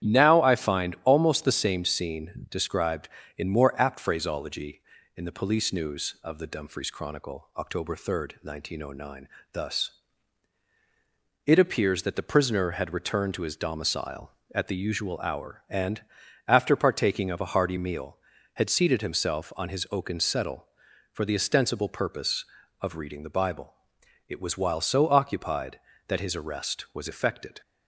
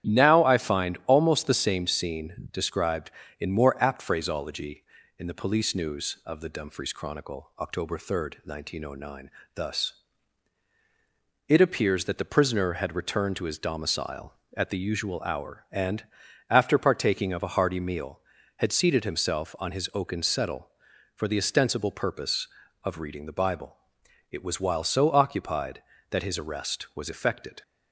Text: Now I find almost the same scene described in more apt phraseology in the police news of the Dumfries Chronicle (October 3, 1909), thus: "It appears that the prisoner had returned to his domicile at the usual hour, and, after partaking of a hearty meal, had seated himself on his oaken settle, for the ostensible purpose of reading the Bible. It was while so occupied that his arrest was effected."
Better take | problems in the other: neither | starts louder than the rest; strong; the same in both

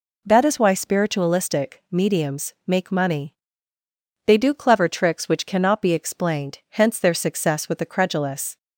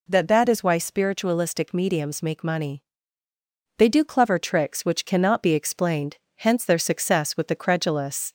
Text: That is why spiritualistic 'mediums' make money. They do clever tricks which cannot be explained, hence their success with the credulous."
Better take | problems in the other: first | says "That" twice; at 0.2 s

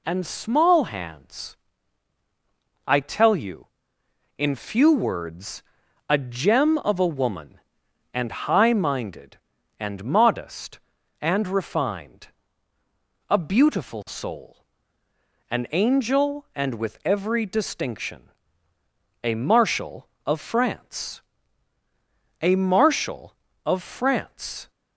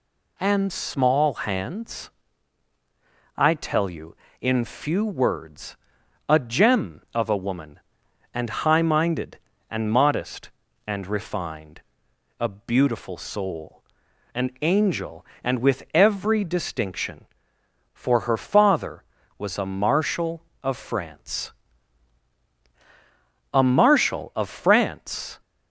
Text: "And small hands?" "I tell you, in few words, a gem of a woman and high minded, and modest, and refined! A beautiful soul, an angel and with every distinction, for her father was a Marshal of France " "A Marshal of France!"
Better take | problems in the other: second | skips "for her father was"; at 18.7 s

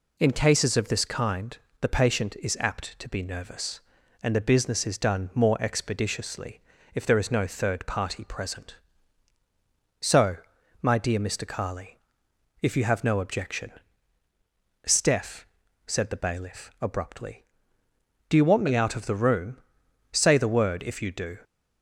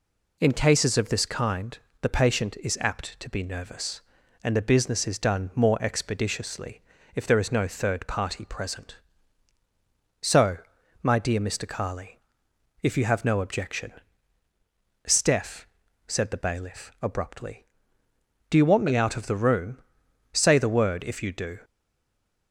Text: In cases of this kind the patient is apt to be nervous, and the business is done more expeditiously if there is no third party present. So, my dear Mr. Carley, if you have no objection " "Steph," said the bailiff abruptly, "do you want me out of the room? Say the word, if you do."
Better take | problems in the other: first | pauses between "kind" and "the"; slight; at 1.7 s; 0.24 s long; slight in the first // pauses between "expeditiously" and "if"; slight; at 6.7 s; 0.36 s long; slight in the first // stays silent after the last word; slight; from 21.6 s on; 0.9 s long

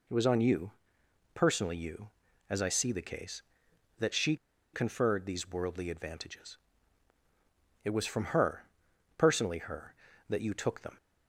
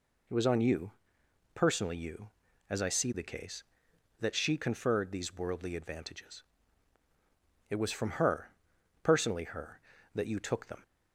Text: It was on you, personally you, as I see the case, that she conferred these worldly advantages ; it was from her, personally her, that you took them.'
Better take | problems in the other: second | pauses between "she" and "conferred"; at 4.3 s; 0.38 s long

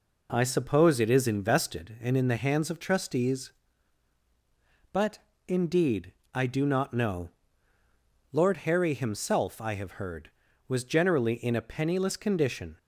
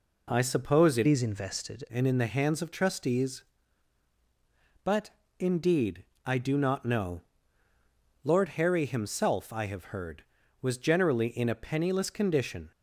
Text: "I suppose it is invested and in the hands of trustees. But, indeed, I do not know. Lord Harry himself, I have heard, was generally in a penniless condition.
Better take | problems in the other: first | changes voice from "is" to "invested"; from 1.0 to 1.8 s; 0.8 s long

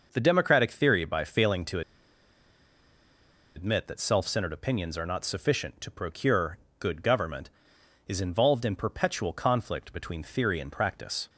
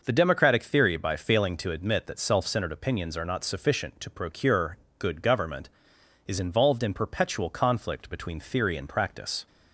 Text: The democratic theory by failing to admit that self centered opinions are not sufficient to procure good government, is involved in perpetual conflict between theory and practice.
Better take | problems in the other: second | pauses between "to" and "admit"; strong; at 1.8 s; 1.7 s long // pauses between "procure" and "good"; slight; at 6.5 s; 0.20 s long; slight in the second

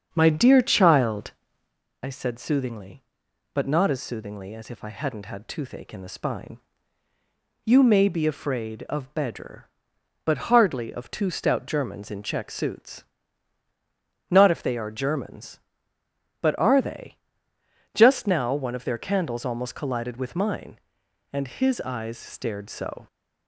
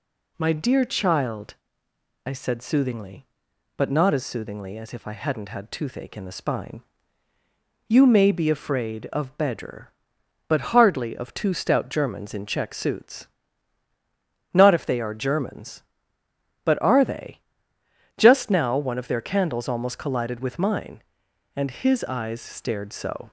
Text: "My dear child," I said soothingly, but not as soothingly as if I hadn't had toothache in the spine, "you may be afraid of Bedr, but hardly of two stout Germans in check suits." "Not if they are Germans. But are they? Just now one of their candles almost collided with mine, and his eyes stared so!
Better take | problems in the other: second | starts louder than the rest; until 1.8 s; 7 dB

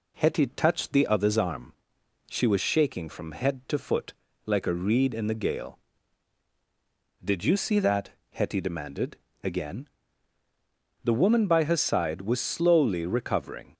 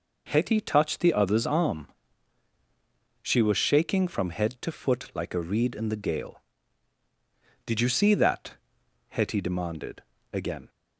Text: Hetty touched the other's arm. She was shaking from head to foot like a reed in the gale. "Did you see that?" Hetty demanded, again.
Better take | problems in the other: second | pauses between "foot" and "like"; slight; at 4.1 s; 0.32 s long // goes on to say "The woman by her side was slowly recovering"; strong; from 11.0 s on; 2.7 s long

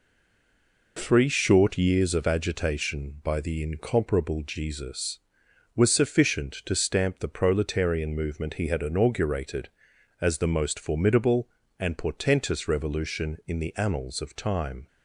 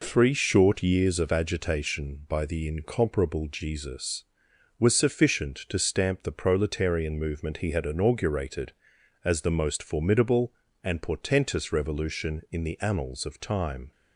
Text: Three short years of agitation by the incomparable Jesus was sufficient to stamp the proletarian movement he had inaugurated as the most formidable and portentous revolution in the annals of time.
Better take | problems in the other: second | stays silent before the first word; slight; until 0.9 s; 0.9 s long

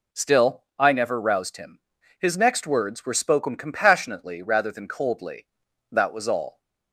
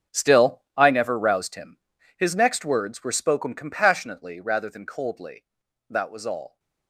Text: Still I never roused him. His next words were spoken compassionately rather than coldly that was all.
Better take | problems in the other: first | gets quieter; strong; throughout; 14.5 dB // pauses between "Still" and "I"; slight; at 0.6 s; 0.16 s long; slight in the first

